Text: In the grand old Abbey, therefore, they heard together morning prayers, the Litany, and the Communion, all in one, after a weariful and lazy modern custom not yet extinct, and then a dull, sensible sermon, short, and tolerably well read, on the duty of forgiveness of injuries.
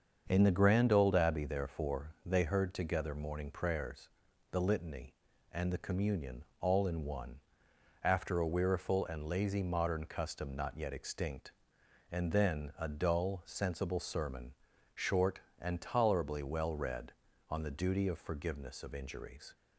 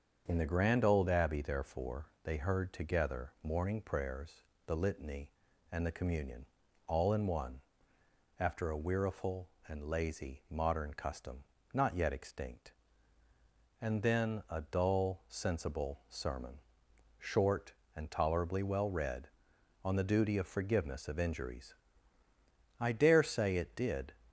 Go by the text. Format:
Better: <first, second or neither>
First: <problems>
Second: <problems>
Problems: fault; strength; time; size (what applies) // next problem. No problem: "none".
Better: first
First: starts louder than the rest; until 1.2 s; 7 dB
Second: starts louder than the rest; until 1.2 s; 6.5 dB // pauses between "custom" and "not"; slight; at 11.4 s; 0.28 s long // goes on to say "I dare say it did"; from 22.8 s on; 1.3 s long